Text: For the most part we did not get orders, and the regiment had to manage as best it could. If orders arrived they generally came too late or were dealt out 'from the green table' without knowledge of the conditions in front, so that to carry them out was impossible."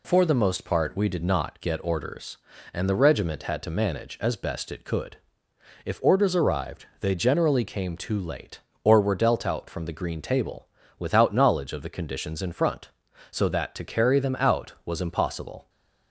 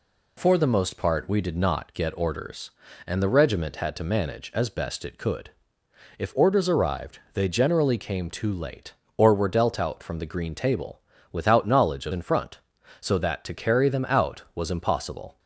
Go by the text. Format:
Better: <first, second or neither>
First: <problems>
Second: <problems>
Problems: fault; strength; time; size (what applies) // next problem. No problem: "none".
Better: first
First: pauses between "arrived" and "they"; slight; at 6.8 s; 0.16 s long // pauses between "table" and "without"; slight; at 10.6 s; 0.32 s long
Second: pauses between "arrived" and "they"; slight; at 7.1 s; 0.16 s long // pauses between "table" and "without"; slight; at 11.0 s; 0.32 s long // skips "the conditions"; at 12.1 s